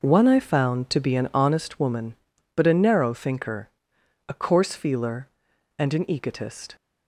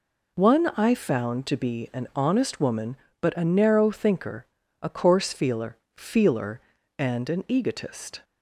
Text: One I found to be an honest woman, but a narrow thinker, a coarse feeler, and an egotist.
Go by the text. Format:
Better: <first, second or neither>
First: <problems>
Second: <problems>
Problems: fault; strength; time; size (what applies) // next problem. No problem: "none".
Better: first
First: none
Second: says "feeler" twice; at 5.9 s